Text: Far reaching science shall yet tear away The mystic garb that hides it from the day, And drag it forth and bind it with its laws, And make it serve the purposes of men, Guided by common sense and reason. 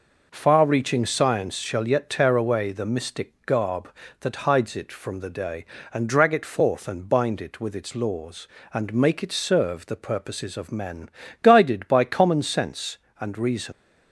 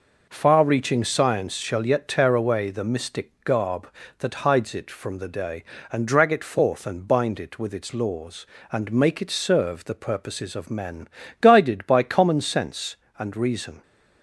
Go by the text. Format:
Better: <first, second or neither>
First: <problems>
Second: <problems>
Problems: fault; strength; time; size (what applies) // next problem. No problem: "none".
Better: second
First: leaves "reason" unfinished; at 13.7 s; 110 ms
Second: none